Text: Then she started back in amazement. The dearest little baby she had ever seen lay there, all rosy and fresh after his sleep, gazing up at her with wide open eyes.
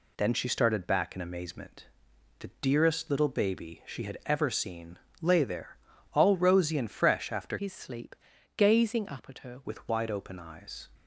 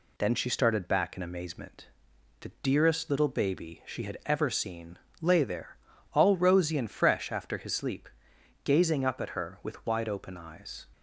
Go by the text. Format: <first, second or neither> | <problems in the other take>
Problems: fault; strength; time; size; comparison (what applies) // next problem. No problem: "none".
second | pauses between "seen" and "lay"; slight; at 4.9 s; 0.24 s long; slight in the second // changes voice from "his" to "her"; from 7.5 to 9.6 s; 2.1 s long